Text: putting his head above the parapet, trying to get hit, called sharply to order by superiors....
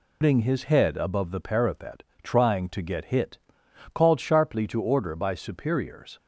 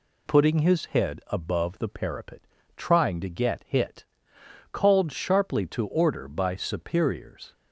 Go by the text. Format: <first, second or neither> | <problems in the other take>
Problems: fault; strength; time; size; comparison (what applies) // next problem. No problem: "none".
second | loses the start of "putting"; at 0.2 s; 110 ms